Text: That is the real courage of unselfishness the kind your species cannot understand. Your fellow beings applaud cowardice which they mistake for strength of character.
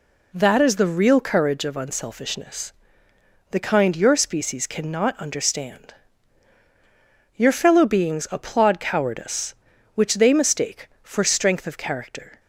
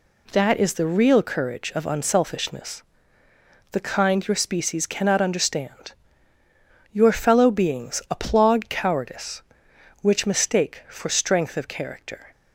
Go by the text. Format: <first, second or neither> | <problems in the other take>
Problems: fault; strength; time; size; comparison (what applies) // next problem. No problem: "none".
first | pauses between "unselfishness" and "the"; noticeable; at 2.8 s; 0.90 s long; noticeable in the first // skips "they"; at 10.2 s